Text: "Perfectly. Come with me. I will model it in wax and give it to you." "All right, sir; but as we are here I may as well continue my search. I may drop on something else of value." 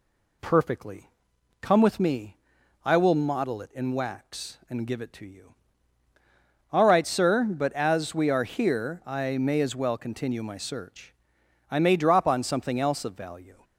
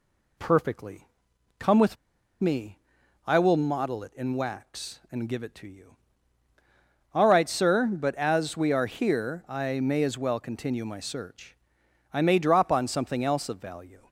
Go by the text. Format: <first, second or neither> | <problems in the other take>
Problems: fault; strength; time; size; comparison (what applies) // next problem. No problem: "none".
first | pauses between "with" and "me"; at 1.9 s; 0.44 s long